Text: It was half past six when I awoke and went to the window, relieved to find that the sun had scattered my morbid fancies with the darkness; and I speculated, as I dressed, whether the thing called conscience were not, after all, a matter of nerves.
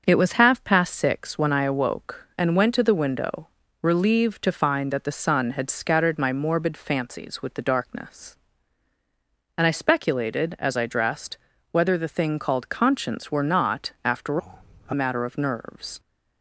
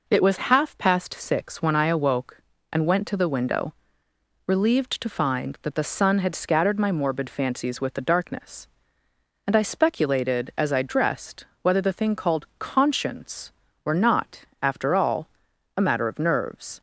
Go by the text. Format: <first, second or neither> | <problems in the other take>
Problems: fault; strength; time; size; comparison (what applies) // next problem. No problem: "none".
second | starts louder than the rest; until 1.0 s; 6.5 dB // changes voice from "all" to "a"; from 14.3 to 14.9 s; 0.6 s long